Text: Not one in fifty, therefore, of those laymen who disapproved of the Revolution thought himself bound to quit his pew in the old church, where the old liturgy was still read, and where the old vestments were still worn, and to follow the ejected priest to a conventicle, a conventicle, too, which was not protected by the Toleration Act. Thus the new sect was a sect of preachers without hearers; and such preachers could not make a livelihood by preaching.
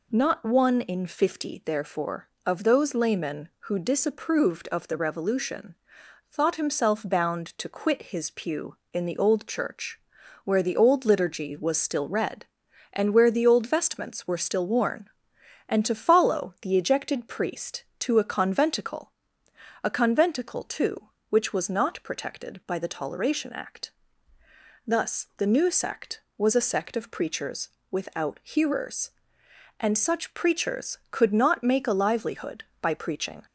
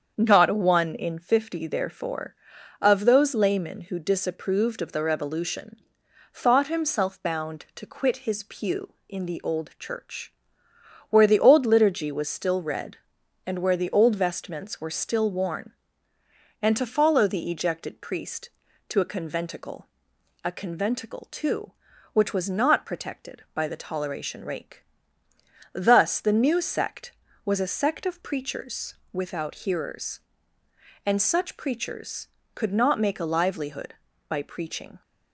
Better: first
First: pauses between "Revolution" and "thought"; noticeable; at 5.7 s; 0.56 s long // pauses between "preachers" and "without"; slight; at 27.7 s; 0.20 s long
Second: starts louder than the rest; strong; until 1.1 s; 7.5 dB // pauses between "Revolution" and "thought"; noticeable; at 5.7 s; 0.56 s long // says "Rake" for "Act"; at 24.4 s // pauses between "preachers" and "without"; slight; at 28.9 s; 0.18 s long

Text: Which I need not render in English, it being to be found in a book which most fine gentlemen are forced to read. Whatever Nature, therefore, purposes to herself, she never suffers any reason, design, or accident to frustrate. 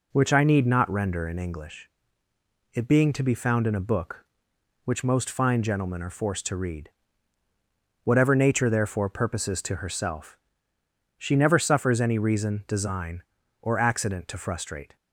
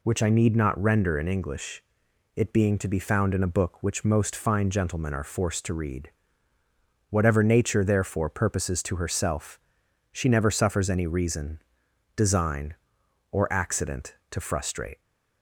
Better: neither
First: none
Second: none

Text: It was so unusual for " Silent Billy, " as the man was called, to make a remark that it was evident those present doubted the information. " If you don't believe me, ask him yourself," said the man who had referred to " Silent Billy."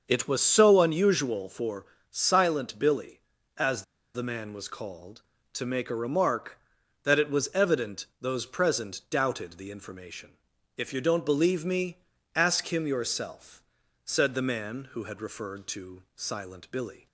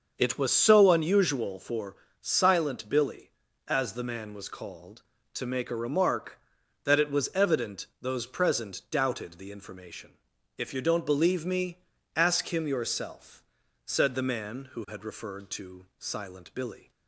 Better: second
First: starts louder than the rest; until 1.0 s; 6 dB // pauses between "as" and "the"; slight; at 3.8 s; 0.31 s long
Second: starts louder than the rest; until 1.1 s; 6.5 dB

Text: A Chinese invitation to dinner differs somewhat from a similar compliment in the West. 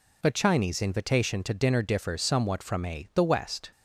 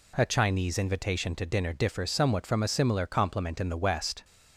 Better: second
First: skips "similar compliment in"; at 3.1 s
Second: none

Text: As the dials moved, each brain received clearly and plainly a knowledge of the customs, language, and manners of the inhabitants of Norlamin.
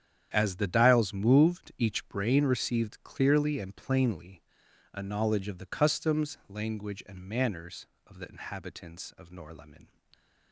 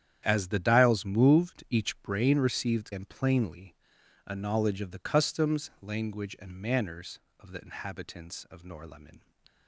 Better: first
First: starts louder than the rest; strong; until 1.3 s; 9 dB // pauses between "plainly" and "a"; noticeable; at 4.4 s; 0.54 s long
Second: starts louder than the rest; strong; until 1.2 s; 9.5 dB // skips "clearly"; at 2.9 s // pauses between "plainly" and "a"; noticeable; at 3.7 s; 0.54 s long

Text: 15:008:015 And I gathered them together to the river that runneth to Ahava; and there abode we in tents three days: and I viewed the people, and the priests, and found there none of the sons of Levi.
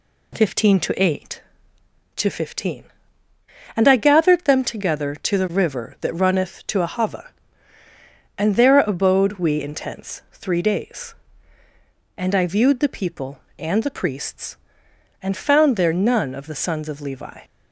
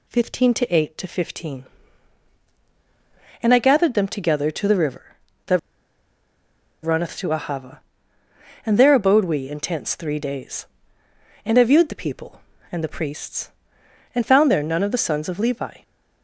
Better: first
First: none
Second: pauses between "that" and "runneth"; at 5.5 s; 1.2 s long

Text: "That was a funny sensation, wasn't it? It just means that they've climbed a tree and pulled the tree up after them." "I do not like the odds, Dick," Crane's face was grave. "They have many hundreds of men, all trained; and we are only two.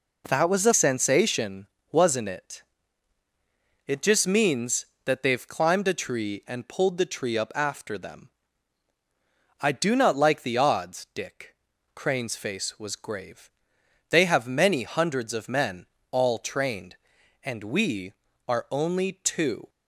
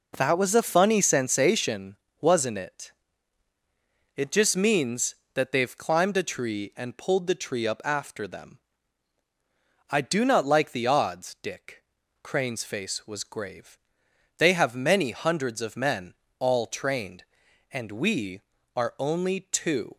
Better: second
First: skips "funny"; at 0.7 s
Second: none

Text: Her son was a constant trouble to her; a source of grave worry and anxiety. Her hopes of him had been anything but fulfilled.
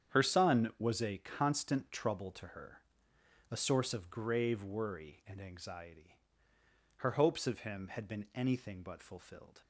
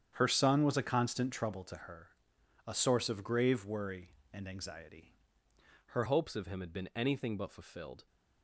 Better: first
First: starts louder than the rest; strong; until 1.2 s; 8.5 dB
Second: starts louder than the rest; strong; until 1.1 s; 8.5 dB // changes voice at "hopes"; from 6.0 s on; 2.0 s long

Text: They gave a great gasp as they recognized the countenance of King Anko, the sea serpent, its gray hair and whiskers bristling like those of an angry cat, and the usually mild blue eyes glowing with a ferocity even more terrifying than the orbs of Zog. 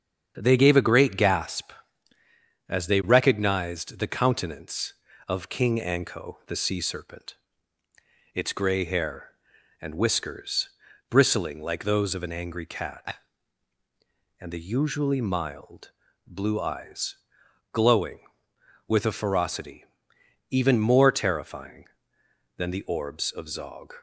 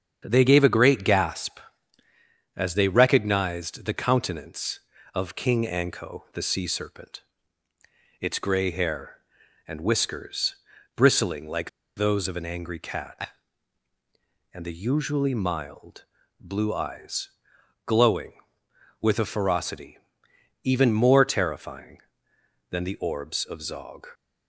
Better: first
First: starts louder than the rest; strong; until 1.3 s; 8 dB // pauses between "whiskers" and "bristling"; at 10.6 s; 0.40 s long // pauses between "mild" and "blue"; at 15.8 s; 0.38 s long // pauses between "eyes" and "glowing"; noticeable; at 17.1 s; 0.56 s long // pauses between "ferocity" and "even"; noticeable; at 19.8 s; 0.66 s long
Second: starts louder than the rest; strong; until 1.2 s; 8 dB // pauses between "whiskers" and "bristling"; at 10.5 s; 0.40 s long // pauses between "like" and "those"; slight; at 11.6 s; 0.28 s long // pauses between "mild" and "blue"; at 16.0 s; 0.38 s long // pauses between "eyes" and "glowing"; noticeable; at 17.2 s; 0.56 s long // pauses between "ferocity" and "even"; noticeable; at 19.9 s; 0.66 s long

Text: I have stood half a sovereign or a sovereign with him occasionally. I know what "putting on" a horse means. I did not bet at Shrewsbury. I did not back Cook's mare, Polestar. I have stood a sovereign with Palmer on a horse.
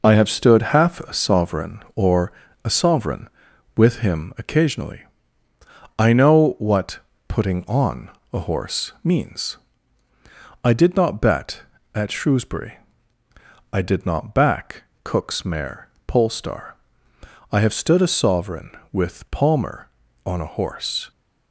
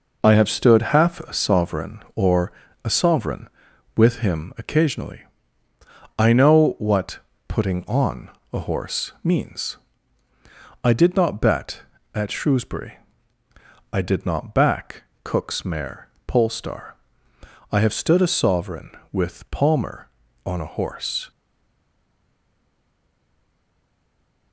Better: first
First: pauses between "or" and "a"; slight; at 2.3 s; 0.32 s long // pauses between "what" and "putting"; slight; at 7.0 s; 0.28 s long // pauses between "on" and "a"; slight; at 8.0 s; 0.24 s long // pauses between "back" and "Cook's"; slight; at 14.8 s; 0.18 s long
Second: pauses between "or" and "a"; slight; at 2.5 s; 0.32 s long // pauses between "what" and "putting"; slight; at 7.2 s; 0.28 s long // pauses between "on" and "a"; slight; at 8.2 s; 0.24 s long // pauses between "back" and "Cook's"; slight; at 15.0 s; 0.18 s long // stays silent after the last word; strong; from 21.3 s on; 3.2 s long

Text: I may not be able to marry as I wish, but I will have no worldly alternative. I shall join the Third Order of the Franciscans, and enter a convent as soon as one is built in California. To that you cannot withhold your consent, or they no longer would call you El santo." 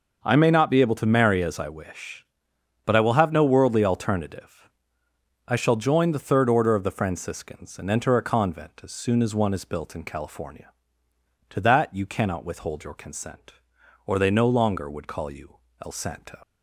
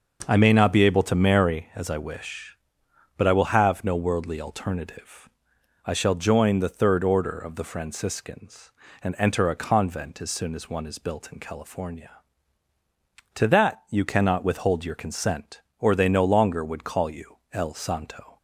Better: second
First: pauses between "you" and "El"; slight; at 15.5 s; 0.28 s long // leaves "santo" unfinished; at 16.4 s; 65 ms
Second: none

